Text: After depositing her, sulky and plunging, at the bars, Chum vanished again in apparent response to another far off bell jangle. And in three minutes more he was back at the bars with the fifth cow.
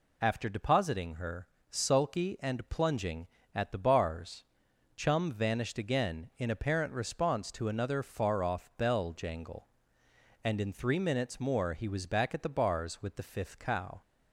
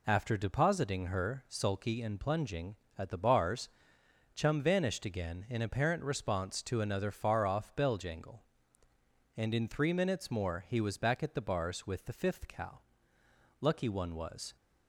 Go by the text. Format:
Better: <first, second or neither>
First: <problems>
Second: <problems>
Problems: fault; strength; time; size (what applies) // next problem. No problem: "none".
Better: first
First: none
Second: goes on to say "Lucky one was"; noticeable; from 13.5 s on; 0.96 s long